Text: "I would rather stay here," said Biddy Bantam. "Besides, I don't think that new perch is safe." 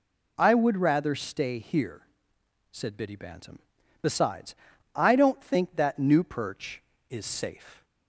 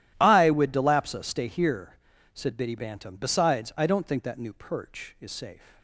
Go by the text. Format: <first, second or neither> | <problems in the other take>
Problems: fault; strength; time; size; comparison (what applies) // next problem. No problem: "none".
first | starts louder than the rest; strong; until 1.2 s; 13 dB // says "delapsa" for "rather"; at 0.7 s